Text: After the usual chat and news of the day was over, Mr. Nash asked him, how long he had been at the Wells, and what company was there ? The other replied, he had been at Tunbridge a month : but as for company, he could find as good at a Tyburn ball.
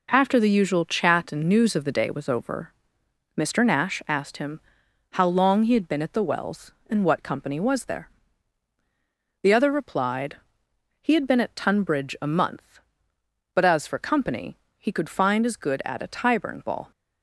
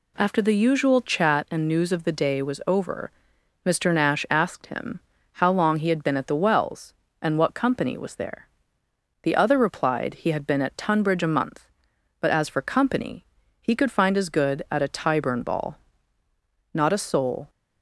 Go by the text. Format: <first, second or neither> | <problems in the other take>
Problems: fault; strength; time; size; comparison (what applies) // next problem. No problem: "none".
first | goes on to say "Not a soul"; noticeable; from 16.7 s on; 0.76 s long